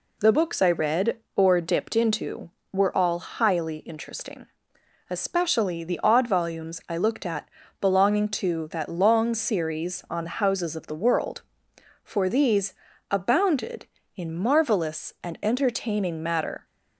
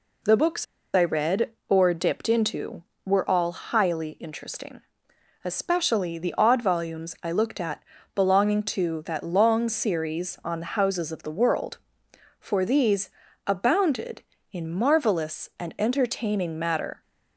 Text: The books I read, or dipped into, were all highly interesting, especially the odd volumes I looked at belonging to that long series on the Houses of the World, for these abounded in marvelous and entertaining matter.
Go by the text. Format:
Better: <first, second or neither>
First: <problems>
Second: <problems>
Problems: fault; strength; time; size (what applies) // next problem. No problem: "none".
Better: first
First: pauses between "at" and "belonging"; slight; at 7.4 s; 0.36 s long // pauses between "these" and "abounded"; slight; at 12.7 s; 0.36 s long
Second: pauses between "books" and "I"; slight; at 0.6 s; 0.29 s long // pauses between "at" and "belonging"; slight; at 7.8 s; 0.36 s long // pauses between "these" and "abounded"; slight; at 13.1 s; 0.36 s long